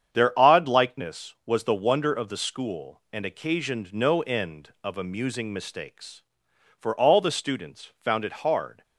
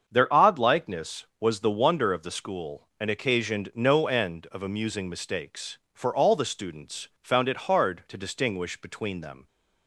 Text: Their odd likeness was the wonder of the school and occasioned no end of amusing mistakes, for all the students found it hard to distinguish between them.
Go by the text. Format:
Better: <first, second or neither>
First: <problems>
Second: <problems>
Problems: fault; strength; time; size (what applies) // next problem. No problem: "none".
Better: second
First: starts louder than the rest; strong; until 1.1 s; 8 dB // stops before "to distinguish between them"; at 8.8 s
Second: starts louder than the rest; until 1.0 s; 7 dB